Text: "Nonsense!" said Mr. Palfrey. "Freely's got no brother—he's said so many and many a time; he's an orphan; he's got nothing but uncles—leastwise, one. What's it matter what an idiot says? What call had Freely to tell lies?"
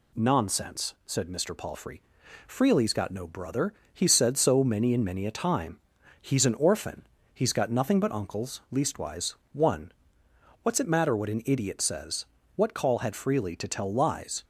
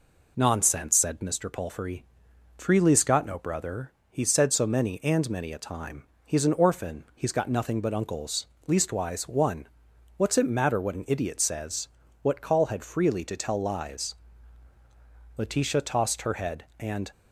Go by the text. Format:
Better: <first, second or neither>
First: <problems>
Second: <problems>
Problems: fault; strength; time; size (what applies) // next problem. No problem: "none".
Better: first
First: none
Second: goes on to say "Letitia tossed her head and"; strong; from 15.3 s on; 1.7 s long